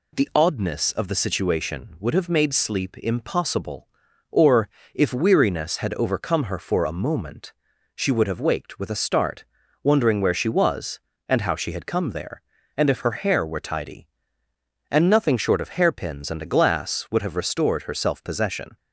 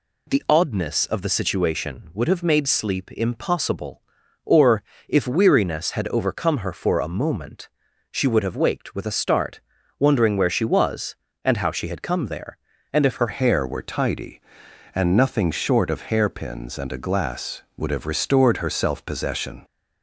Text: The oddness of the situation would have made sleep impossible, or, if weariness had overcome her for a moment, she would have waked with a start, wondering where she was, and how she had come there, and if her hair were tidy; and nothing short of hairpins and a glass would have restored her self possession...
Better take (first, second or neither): first